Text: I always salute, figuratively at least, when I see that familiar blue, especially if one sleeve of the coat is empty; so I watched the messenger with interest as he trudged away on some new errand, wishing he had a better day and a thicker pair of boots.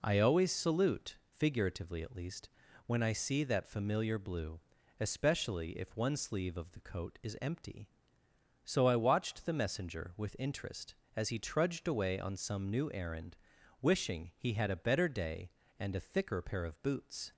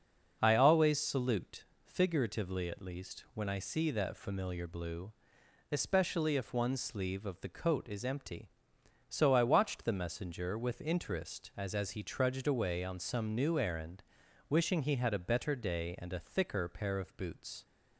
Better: first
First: none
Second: starts louder than the rest; until 1.4 s; 6 dB // says "as" twice; at 11.7 s

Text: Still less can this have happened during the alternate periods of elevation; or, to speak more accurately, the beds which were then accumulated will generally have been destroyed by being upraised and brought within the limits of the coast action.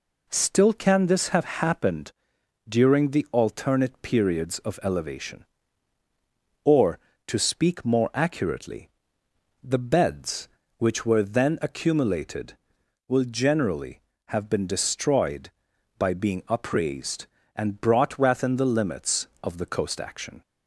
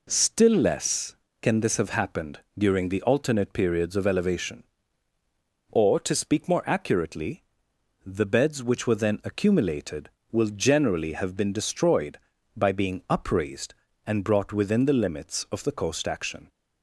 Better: second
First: skips "less"; at 0.7 s // pauses between "happened" and "during"; noticeable; at 2.1 s; 0.56 s long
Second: pauses between "happened" and "during"; slight; at 2.3 s; 0.18 s long

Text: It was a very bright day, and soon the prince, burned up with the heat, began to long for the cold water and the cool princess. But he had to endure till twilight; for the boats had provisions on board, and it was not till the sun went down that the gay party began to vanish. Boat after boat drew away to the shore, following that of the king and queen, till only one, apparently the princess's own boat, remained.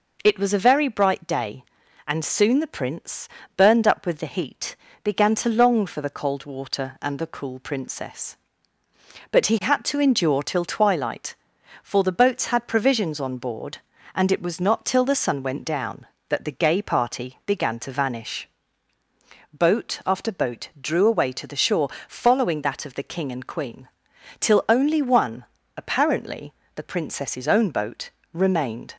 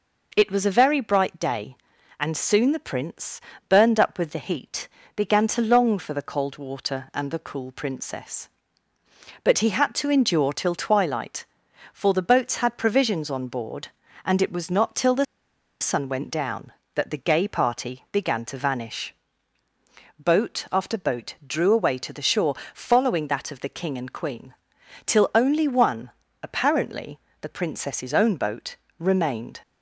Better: first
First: pauses between "apparently" and "the"; slight; at 26.5 s; 0.24 s long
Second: pauses between "the" and "sun"; noticeable; at 15.2 s; 0.57 s long // pauses between "apparently" and "the"; slight; at 27.1 s; 0.24 s long

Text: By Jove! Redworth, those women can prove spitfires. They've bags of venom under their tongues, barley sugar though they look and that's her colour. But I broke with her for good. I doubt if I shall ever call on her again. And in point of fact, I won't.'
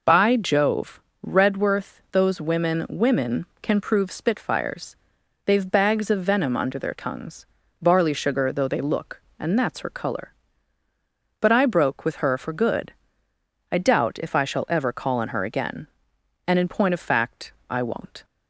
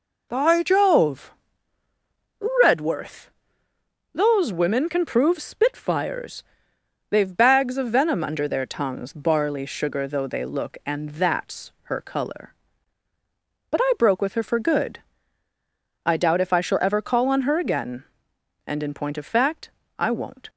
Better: second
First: says "women" twice; at 2.8 s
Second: none

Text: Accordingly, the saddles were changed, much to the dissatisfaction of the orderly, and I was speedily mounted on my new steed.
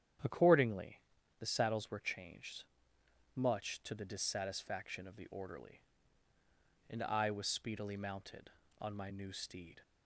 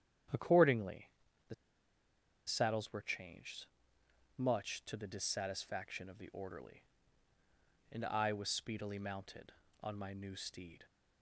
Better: first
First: starts louder than the rest; strong; until 1.6 s; 9.5 dB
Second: starts louder than the rest; strong; until 2.6 s; 9.5 dB // pauses between "the" and "saddles"; noticeable; at 1.5 s; 0.92 s long

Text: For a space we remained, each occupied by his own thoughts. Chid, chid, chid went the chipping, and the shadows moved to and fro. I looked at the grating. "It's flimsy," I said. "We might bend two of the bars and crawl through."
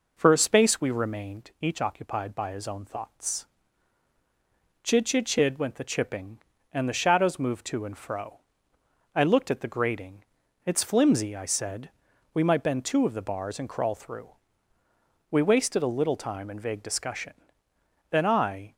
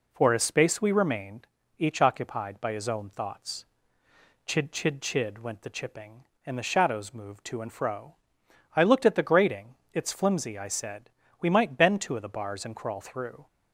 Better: second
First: goes on to say "We wasted a little time in vague discussion Then I"; strong; from 15.2 s on; 3.4 s long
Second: none

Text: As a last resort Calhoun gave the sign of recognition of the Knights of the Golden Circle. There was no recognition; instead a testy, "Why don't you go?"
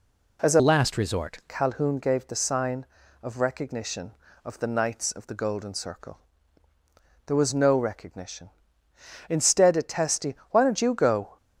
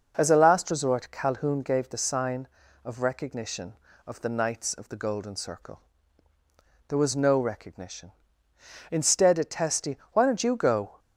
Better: second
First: changes voice from "last" to "resort"; from 0.5 to 1.3 s; 0.8 s long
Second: none

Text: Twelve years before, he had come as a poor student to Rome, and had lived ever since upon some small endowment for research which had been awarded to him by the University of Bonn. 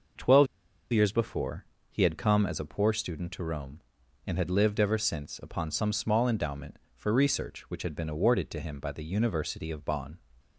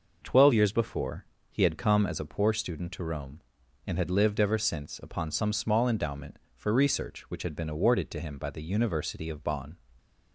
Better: second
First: pauses between "Twelve" and "years"; noticeable; at 0.4 s; 0.46 s long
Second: none

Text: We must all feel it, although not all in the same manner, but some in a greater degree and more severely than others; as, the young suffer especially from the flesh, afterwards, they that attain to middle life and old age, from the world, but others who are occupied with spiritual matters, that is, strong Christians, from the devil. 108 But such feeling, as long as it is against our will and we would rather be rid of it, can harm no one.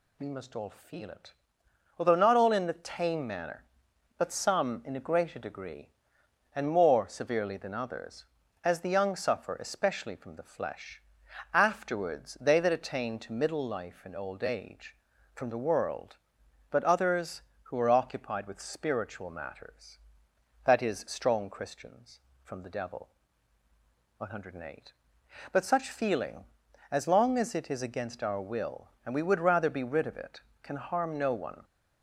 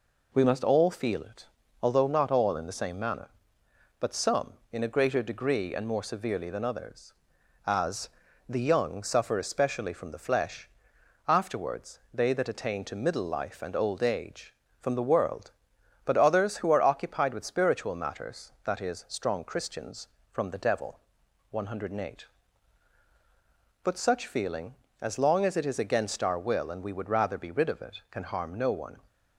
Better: second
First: says "tame" for "same"; at 2.7 s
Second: none

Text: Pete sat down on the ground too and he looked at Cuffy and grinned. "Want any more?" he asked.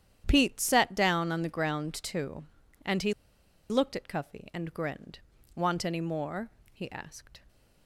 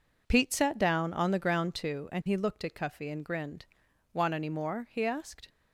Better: second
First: starts louder than the rest; strong; until 1.2 s; 10 dB // pauses between "he" and "looked"; noticeable; at 3.1 s; 0.56 s long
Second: none

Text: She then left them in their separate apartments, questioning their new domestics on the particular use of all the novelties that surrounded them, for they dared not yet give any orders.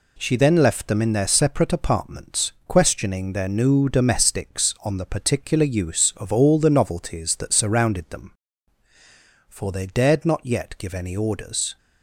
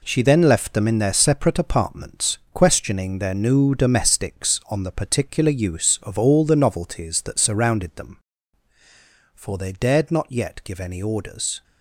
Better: first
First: none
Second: gets quieter; strong; throughout; 9.5 dB

